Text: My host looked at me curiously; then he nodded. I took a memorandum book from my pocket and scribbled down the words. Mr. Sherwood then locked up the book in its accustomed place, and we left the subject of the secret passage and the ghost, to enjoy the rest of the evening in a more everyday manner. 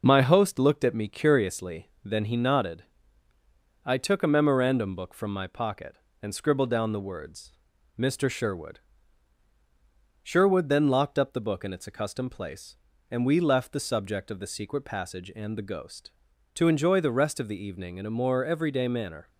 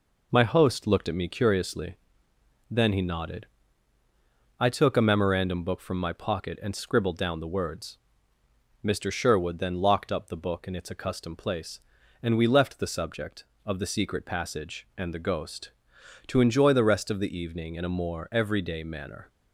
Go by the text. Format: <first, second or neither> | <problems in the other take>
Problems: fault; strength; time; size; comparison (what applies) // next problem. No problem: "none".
second | says "Sherwood" twice; at 10.2 s